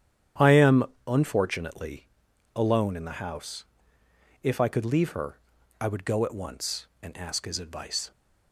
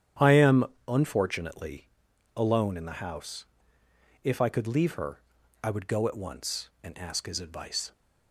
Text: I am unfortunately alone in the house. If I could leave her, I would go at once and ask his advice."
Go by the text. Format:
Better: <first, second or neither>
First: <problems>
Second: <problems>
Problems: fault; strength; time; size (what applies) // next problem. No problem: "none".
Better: neither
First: starts louder than the rest; strong; until 1.6 s; 10 dB // pauses between "am" and "unfortunately"; slight; at 0.8 s; 0.22 s long // pauses between "unfortunately" and "alone"; noticeable; at 2.0 s; 0.46 s long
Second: starts louder than the rest; strong; until 1.4 s; 10 dB // pauses between "am" and "unfortunately"; slight; at 0.6 s; 0.22 s long // pauses between "unfortunately" and "alone"; noticeable; at 1.8 s; 0.46 s long